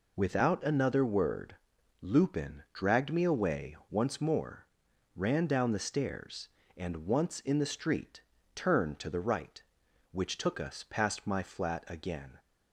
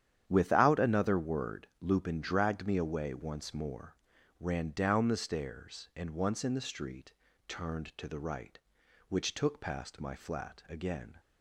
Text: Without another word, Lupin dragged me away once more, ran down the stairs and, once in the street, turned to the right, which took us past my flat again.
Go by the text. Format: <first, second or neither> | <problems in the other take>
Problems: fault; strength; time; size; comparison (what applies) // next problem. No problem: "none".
first | starts louder than the rest; strong; until 1.2 s; 9.5 dB // skips "us"; at 9.5 s